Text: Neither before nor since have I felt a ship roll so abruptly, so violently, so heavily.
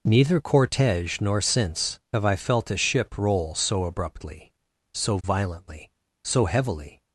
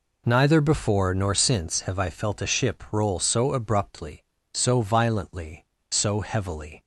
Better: second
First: says "cortege" for "before"; at 0.4 s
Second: none

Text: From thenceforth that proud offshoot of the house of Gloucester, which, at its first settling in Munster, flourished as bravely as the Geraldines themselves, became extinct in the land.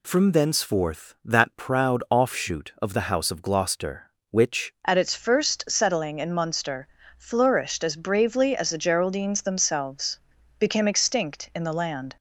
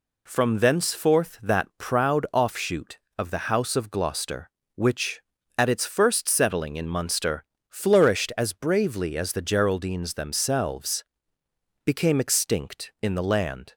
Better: second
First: changes voice at "at"; from 4.8 s on; 7.3 s long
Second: none

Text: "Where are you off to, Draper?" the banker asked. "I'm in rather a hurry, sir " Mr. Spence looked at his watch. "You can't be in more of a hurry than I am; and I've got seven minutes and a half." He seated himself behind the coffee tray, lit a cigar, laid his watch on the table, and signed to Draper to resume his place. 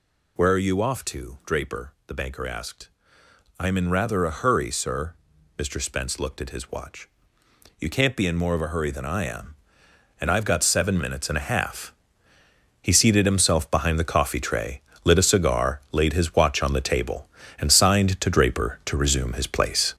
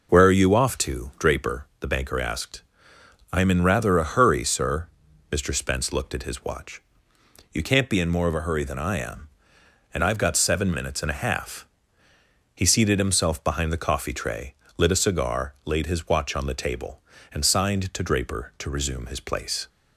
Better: second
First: gets louder; strong; throughout; 8 dB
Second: none

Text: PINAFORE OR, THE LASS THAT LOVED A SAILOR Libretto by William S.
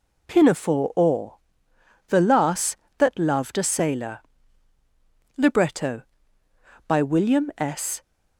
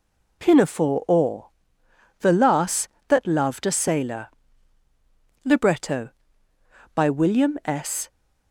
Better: neither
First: pauses between "SAILOR" and "Libretto"; at 4.2 s; 1.1 s long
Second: pauses between "SAILOR" and "Libretto"; at 4.2 s; 1.1 s long

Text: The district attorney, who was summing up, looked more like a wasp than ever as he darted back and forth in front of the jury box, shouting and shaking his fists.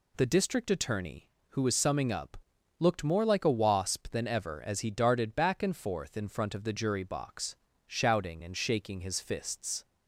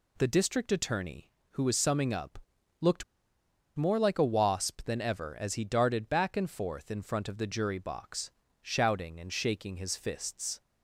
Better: first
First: none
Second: pauses between "looked" and "more"; noticeable; at 3.0 s; 0.73 s long

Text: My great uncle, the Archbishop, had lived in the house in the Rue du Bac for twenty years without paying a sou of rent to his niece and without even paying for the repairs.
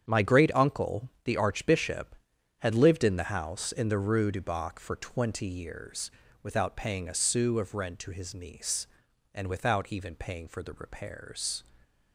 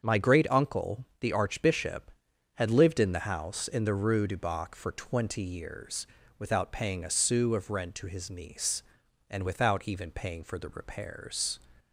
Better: second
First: gets quieter; strong; throughout; 10.5 dB // starts louder than the rest; strong; until 1.0 s; 8.5 dB // pauses between "years" and "without"; slight; at 6.1 s; 0.32 s long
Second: starts louder than the rest; until 1.0 s; 7 dB // pauses between "years" and "without"; slight; at 6.0 s; 0.32 s long

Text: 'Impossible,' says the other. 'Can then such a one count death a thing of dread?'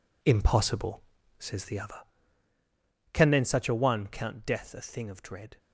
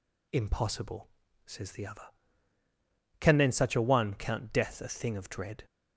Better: second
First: gets quieter; strong; throughout; 10 dB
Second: none

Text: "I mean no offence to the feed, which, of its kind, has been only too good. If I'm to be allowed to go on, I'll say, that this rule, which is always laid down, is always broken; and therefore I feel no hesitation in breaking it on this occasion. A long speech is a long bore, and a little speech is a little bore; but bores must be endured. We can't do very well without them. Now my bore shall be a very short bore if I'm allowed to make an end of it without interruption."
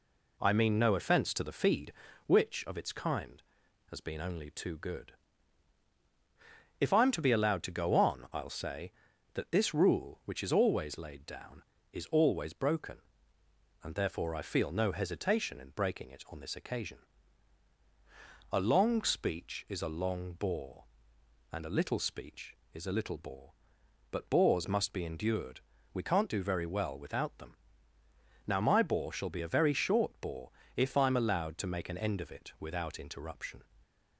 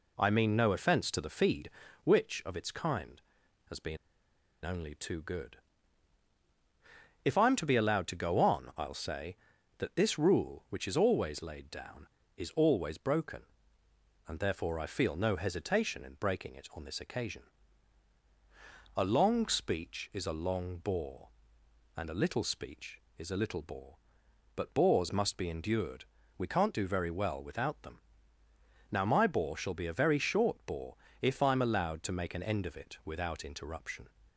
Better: first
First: pauses between "bore" and "if"; slight; at 30.5 s; 0.26 s long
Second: pauses between "been" and "only"; noticeable; at 3.9 s; 0.66 s long // pauses between "bore" and "if"; slight; at 30.9 s; 0.26 s long

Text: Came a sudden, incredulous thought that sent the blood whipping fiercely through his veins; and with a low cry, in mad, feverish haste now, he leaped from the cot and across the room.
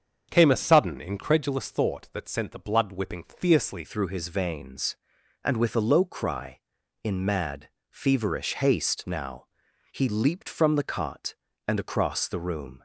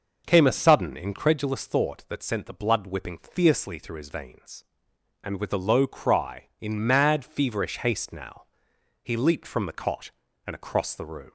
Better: second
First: starts louder than the rest; until 1.3 s; 7 dB // changes voice at "through"; from 3.8 s on; 9.0 s long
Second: none

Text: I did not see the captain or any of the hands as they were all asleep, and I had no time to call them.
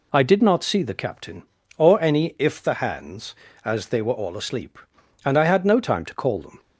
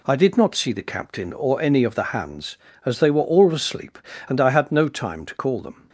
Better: second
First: says "if" for "of"; at 2.3 s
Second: none

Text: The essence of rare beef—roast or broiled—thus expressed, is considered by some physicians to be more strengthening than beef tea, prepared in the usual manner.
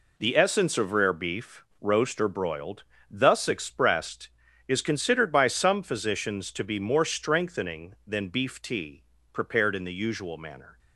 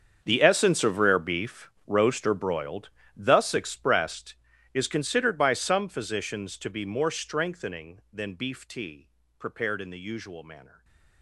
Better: first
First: none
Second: gets quieter; strong; throughout; 17 dB // stays silent after the last word; slight; from 10.6 s on; 0.6 s long

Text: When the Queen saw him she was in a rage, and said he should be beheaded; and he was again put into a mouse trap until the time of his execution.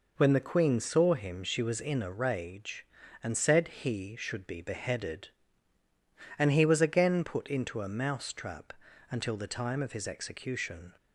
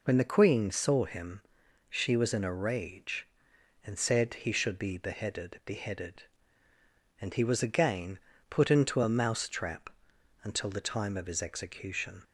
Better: first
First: pauses between "trap" and "until"; slight; at 8.7 s; 0.36 s long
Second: pauses between "him" and "she"; noticeable; at 1.4 s; 0.46 s long // says "beheaded" twice; at 5.6 s // pauses between "again" and "put"; slight; at 8.1 s; 0.32 s long // pauses between "trap" and "until"; noticeable; at 9.9 s; 0.52 s long

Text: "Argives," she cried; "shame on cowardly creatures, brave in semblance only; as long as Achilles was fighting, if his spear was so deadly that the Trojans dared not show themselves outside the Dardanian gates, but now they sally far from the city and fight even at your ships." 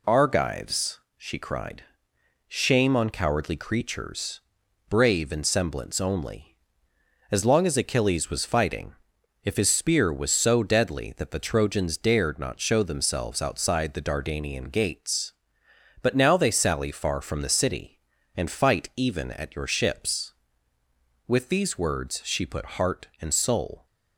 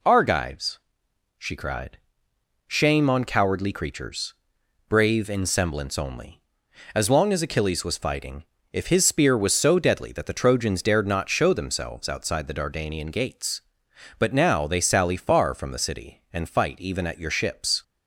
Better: second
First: goes on to say "With these words she put heart and soul"; strong; from 21.2 s on; 2.5 s long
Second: none

